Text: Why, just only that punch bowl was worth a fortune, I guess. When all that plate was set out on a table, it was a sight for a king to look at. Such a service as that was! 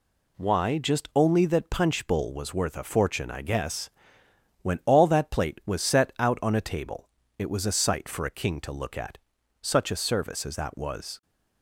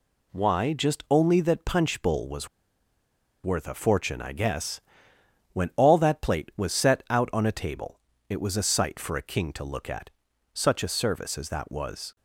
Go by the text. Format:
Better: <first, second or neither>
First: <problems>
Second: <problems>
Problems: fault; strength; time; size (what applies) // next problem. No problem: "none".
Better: first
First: none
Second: pauses between "was" and "worth"; noticeable; at 2.4 s; 0.97 s long